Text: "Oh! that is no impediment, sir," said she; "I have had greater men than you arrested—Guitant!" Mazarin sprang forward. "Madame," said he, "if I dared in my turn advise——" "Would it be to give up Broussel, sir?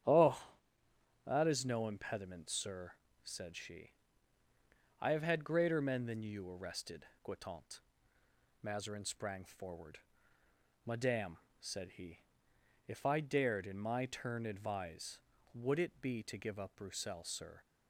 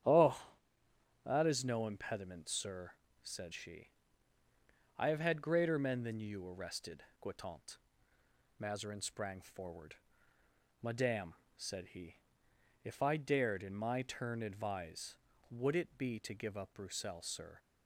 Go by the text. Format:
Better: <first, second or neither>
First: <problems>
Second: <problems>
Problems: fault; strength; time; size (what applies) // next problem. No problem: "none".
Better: neither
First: starts louder than the rest; strong; until 1.8 s; 10 dB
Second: starts louder than the rest; strong; until 1.8 s; 10 dB